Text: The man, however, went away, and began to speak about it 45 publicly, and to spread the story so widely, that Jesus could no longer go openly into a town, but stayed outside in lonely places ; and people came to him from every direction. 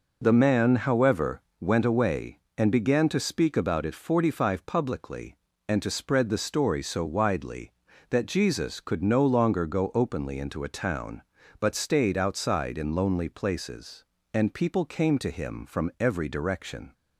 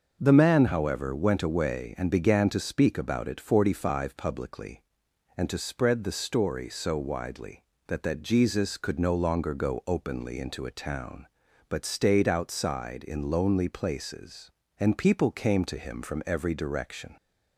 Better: first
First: none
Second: starts louder than the rest; until 1.2 s; 6 dB // says "that" twice; at 8.0 s

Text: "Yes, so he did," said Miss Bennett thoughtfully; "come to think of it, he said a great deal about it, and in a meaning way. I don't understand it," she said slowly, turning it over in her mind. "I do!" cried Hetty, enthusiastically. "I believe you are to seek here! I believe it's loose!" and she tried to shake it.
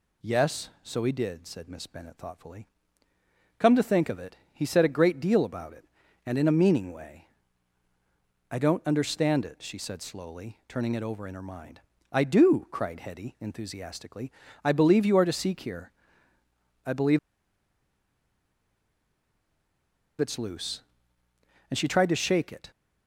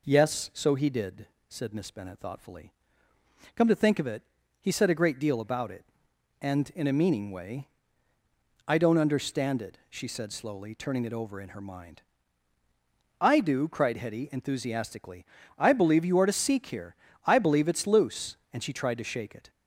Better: second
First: pauses between "believe" and "it's"; strong; at 17.1 s; 3.0 s long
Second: none

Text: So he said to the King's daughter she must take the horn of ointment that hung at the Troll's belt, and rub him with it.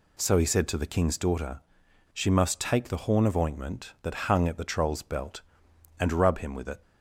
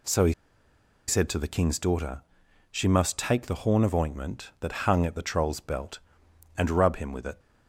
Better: first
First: pauses between "daughter" and "she"; noticeable; at 1.6 s; 0.51 s long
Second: pauses between "he" and "said"; noticeable; at 0.3 s; 0.74 s long // pauses between "daughter" and "she"; noticeable; at 2.2 s; 0.48 s long

